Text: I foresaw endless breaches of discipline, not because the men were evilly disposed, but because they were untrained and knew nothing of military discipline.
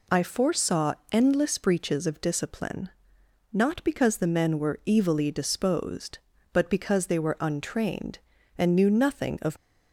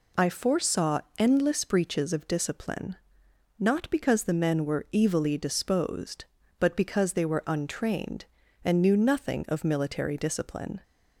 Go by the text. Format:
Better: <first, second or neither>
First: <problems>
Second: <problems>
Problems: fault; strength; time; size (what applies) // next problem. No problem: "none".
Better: second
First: pauses between "foresaw" and "endless"; slight; at 0.9 s; 0.16 s long // stops before "military discipline"; at 9.5 s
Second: pauses between "foresaw" and "endless"; slight; at 1.0 s; 0.16 s long